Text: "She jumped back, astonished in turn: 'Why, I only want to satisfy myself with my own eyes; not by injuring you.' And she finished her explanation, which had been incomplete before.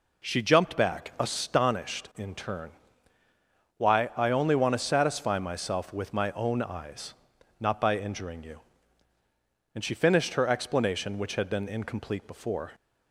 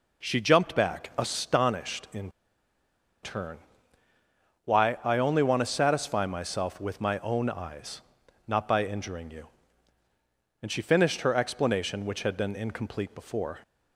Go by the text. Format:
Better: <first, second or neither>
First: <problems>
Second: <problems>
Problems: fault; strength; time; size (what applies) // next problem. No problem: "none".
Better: first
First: none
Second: pauses between "in" and "turn"; noticeable; at 2.2 s; 0.93 s long